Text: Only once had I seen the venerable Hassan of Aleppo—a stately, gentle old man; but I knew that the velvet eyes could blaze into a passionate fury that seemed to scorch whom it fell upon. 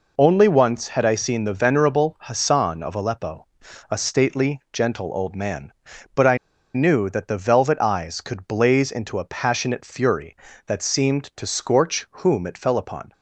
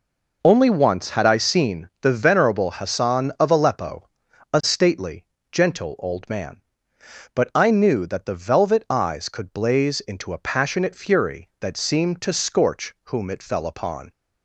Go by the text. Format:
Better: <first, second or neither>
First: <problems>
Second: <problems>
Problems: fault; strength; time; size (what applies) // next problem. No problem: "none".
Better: second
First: pauses between "I" and "knew"; at 6.3 s; 0.38 s long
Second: none